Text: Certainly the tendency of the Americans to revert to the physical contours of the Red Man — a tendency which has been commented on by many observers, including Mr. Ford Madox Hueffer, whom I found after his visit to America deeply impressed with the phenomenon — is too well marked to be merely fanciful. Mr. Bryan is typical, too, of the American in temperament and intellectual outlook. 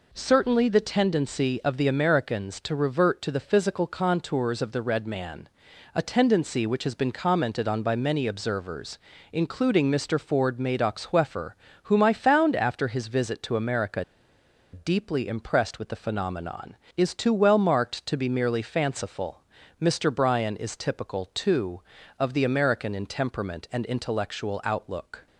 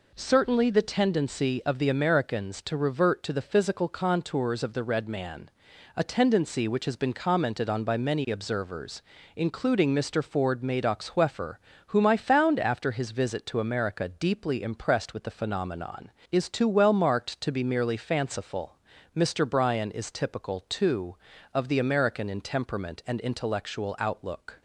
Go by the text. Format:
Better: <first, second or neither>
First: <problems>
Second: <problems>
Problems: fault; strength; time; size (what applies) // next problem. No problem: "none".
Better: second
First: pauses between "America" and "deeply"; noticeable; at 14.0 s; 0.69 s long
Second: none